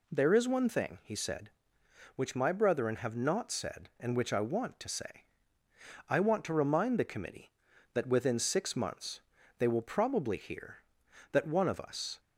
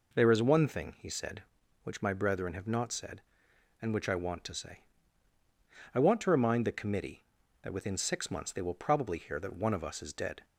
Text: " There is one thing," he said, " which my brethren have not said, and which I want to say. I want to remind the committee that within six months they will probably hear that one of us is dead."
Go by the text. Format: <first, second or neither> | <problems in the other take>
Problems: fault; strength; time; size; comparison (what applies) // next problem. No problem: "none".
second | pauses between "months" and "they"; at 9.2 s; 0.38 s long // stops before "is dead"; at 12.1 s